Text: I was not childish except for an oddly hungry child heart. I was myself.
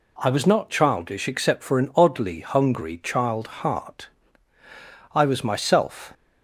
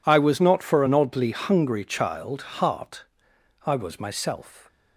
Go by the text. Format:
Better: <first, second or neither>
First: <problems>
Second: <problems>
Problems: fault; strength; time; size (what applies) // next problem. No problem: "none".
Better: first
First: none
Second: skips "childish except"; at 0.6 s